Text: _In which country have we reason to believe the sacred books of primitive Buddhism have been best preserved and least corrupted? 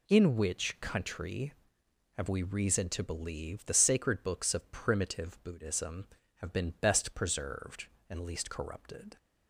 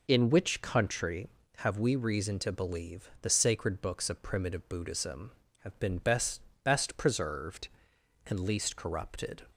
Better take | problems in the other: first | says "best" twice; at 6.6 s

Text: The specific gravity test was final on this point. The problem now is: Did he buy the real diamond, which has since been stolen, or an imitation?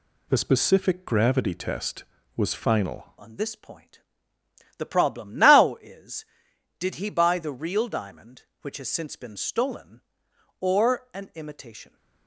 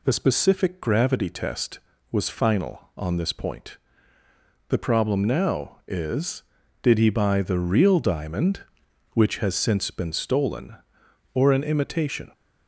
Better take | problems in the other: second | changes voice at "on"; from 3.1 s on; 8.8 s long

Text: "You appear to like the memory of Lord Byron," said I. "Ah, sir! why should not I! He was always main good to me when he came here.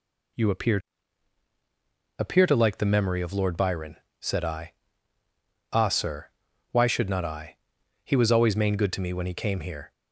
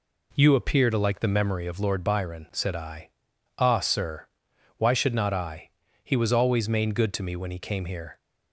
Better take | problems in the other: second | says "appear" twice; at 2.1 s

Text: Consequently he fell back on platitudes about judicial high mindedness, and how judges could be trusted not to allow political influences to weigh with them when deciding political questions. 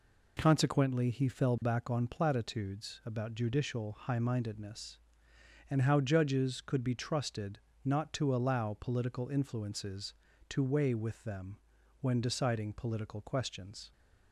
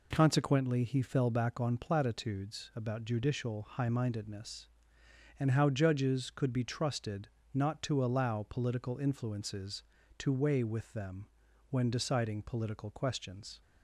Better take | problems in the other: neither | pauses between "trusted" and "not"; slight; the same in both // pauses between "them" and "when"; the same in both

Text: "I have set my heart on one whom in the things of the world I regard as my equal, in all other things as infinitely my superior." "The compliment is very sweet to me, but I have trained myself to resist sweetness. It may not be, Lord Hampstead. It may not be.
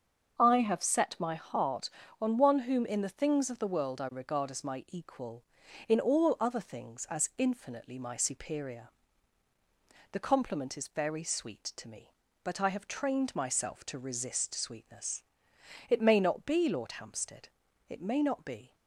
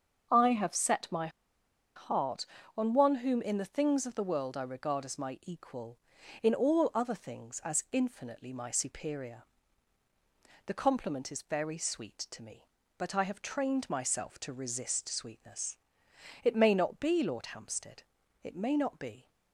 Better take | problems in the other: first | starts louder than the rest; until 1.9 s; 6.5 dB; also in the first // pauses between "my" and "heart"; noticeable; at 1.2 s; 0.67 s long

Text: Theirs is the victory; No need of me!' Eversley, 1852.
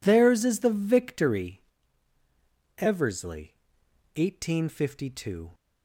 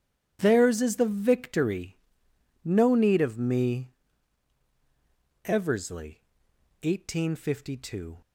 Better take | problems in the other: second | skips "No need of me"; at 2.1 s

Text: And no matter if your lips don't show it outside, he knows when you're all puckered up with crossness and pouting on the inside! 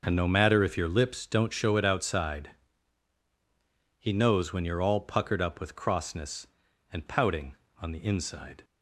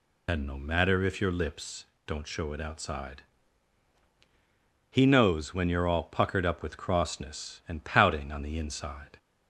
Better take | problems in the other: first | loses the start of "And"; at 0.2 s; 45 ms // pauses between "lips" and "don't"; slight; at 1.8 s; 0.22 s long

